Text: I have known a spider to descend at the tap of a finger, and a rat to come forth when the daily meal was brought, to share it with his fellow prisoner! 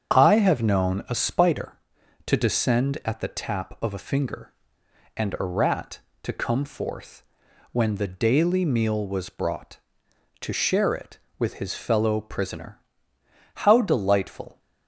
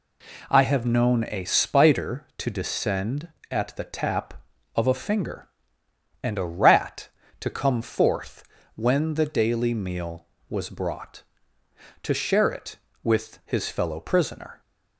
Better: second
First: starts louder than the rest; strong; until 1.1 s; 7.5 dB // pauses between "forth" and "when"; noticeable; at 7.2 s; 0.48 s long // goes on to say "How delightful"; noticeable; from 13.5 s on; 1.0 s long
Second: pauses between "forth" and "when"; slight; at 8.4 s; 0.30 s long

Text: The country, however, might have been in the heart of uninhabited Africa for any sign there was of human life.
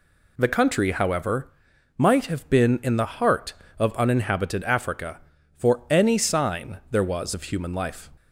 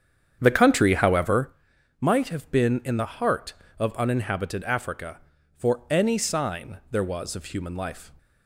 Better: first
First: none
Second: starts louder than the rest; strong; until 1.5 s; 8.5 dB

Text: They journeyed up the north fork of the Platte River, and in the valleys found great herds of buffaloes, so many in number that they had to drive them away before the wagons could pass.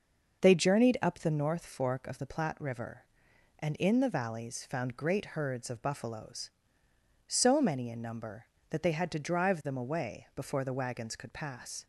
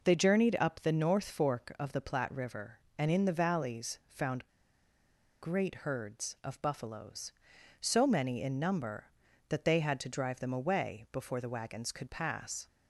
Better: first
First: none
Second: pauses between "found" and "great"; noticeable; at 4.4 s; 0.92 s long

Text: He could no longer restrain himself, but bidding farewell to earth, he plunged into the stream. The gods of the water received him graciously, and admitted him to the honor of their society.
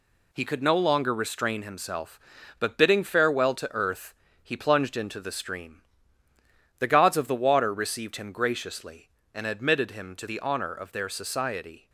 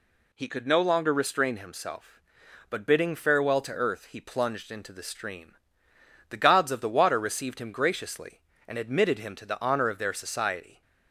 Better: second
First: gets quieter; noticeable; throughout; 6 dB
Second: none

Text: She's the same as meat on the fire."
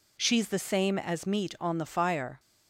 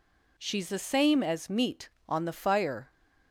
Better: neither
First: none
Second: none

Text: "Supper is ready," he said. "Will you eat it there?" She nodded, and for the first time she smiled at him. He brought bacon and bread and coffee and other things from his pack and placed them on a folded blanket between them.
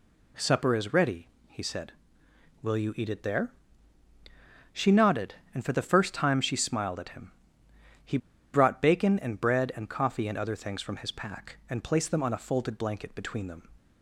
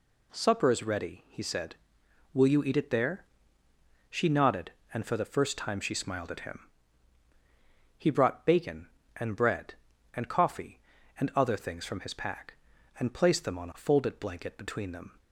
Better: second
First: pauses between "He" and "brought"; at 8.1 s; 0.36 s long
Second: none

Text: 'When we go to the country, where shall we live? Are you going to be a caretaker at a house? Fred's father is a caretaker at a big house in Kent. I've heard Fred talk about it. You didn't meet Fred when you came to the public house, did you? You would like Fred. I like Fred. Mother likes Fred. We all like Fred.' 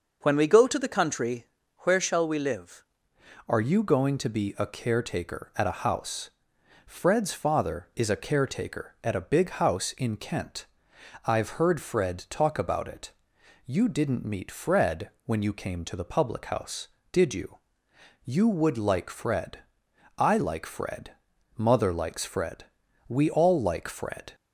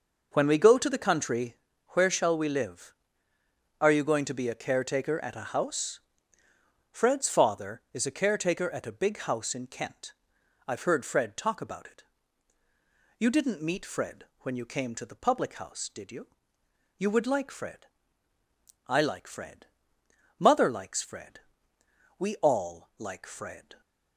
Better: second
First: changes voice at "Are"; from 3.4 s on; 20.9 s long // pauses between "Fred" and "when"; slight; at 15.0 s; 0.16 s long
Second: none

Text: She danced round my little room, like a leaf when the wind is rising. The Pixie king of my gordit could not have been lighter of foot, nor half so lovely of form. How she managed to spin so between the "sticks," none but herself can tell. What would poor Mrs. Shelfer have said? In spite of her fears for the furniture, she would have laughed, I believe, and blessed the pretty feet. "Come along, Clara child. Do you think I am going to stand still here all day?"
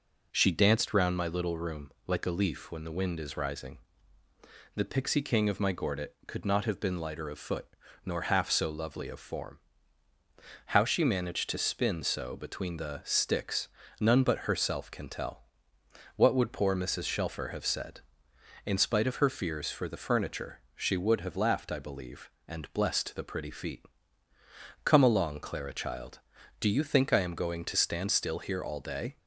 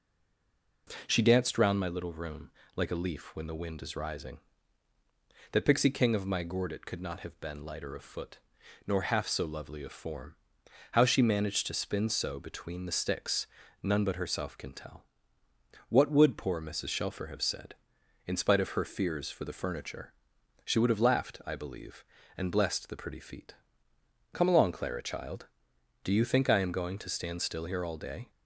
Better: first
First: none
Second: stays silent before the first word; slight; until 0.8 s; 0.8 s long

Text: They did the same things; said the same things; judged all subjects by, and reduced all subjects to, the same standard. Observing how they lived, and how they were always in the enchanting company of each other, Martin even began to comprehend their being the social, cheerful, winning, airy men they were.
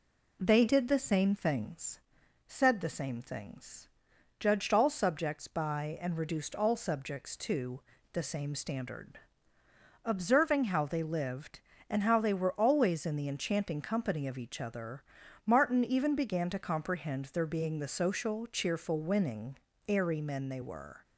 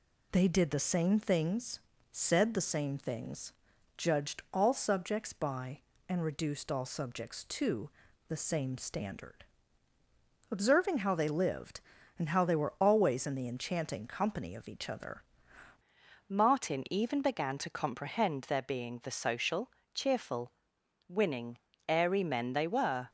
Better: first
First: none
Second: changes voice at "Martin"; from 16.2 s on; 6.8 s long

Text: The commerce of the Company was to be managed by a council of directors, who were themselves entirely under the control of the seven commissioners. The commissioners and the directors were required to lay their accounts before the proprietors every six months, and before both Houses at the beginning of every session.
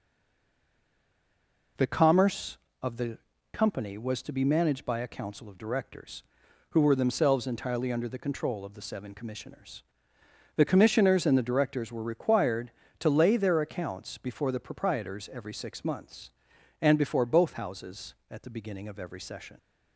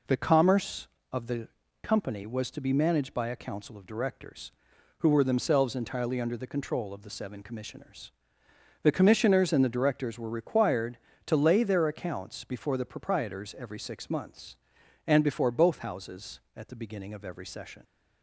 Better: second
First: stays silent before the first word; noticeable; until 1.7 s; 1.7 s long // pauses between "the" and "Company"; slight; at 3.1 s; 0.34 s long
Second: pauses between "the" and "Company"; slight; at 1.4 s; 0.34 s long

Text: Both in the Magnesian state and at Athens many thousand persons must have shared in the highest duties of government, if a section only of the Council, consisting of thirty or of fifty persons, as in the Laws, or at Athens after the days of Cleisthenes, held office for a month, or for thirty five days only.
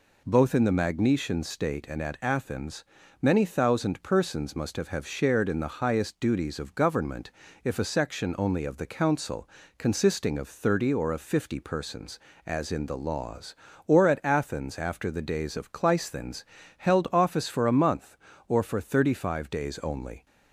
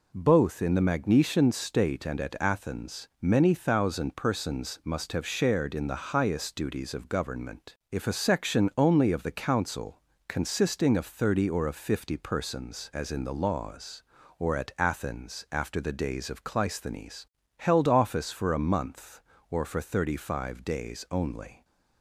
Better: second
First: pauses between "Athens" and "many"; at 2.8 s; 0.38 s long // says "have" twice; at 4.8 s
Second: none

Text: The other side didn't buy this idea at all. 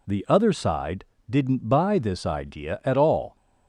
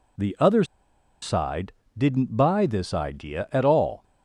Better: first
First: pauses between "side" and "didn't"; slight; at 1.0 s; 0.26 s long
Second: pauses between "other" and "side"; noticeable; at 0.6 s; 0.58 s long // pauses between "side" and "didn't"; slight; at 1.7 s; 0.26 s long

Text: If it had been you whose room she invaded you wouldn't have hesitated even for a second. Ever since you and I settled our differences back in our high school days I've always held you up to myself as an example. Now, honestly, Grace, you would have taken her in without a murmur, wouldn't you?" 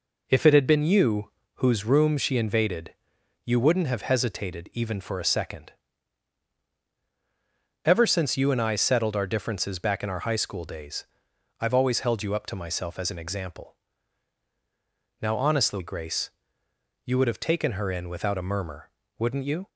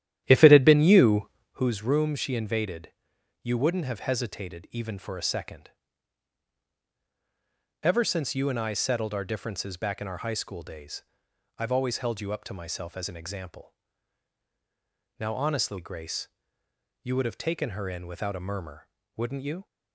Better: first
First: pauses between "you" and "whose"; slight; at 1.2 s; 0.26 s long // pauses between "invaded" and "you"; noticeable; at 2.9 s; 0.54 s long // pauses between "days" and "I've"; noticeable; at 11.0 s; 0.56 s long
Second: starts louder than the rest; strong; until 1.6 s; 11.5 dB // pauses between "you" and "whose"; slight; at 1.2 s; 0.26 s long // pauses between "invaded" and "you"; noticeable; at 2.9 s; 0.54 s long // pauses between "days" and "I've"; noticeable; at 11.0 s; 0.56 s long

